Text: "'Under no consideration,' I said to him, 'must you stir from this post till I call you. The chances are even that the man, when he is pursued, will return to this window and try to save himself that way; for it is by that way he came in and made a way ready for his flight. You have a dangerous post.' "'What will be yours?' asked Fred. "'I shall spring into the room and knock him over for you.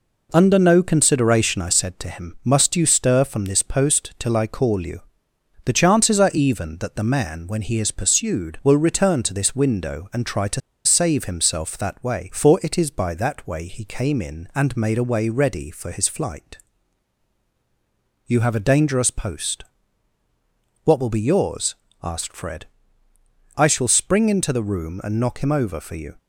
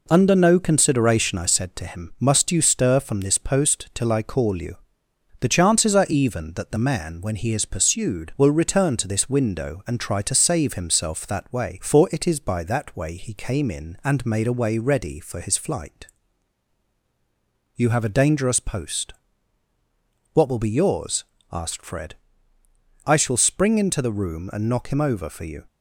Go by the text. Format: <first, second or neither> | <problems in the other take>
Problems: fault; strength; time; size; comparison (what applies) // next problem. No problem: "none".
second | pauses between "to" and "save"; slight; at 10.6 s; 0.24 s long